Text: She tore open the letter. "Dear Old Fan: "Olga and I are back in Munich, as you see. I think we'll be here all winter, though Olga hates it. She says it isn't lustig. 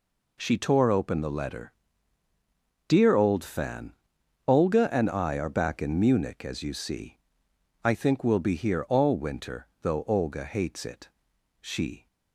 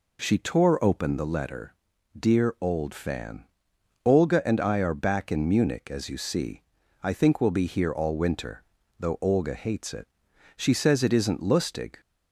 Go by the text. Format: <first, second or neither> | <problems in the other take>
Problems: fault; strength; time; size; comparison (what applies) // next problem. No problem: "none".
second | stops before "says it isn't lustig"; at 12.0 s